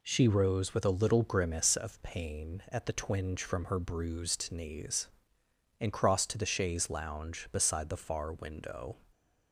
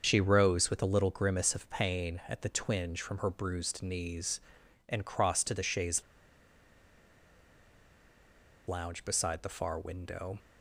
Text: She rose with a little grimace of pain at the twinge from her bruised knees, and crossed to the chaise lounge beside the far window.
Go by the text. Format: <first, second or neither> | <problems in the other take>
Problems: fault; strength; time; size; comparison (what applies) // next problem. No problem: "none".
first | starts louder than the rest; until 1.0 s; 6.5 dB // pauses between "chaise" and "lounge"; strong; at 6.0 s; 2.6 s long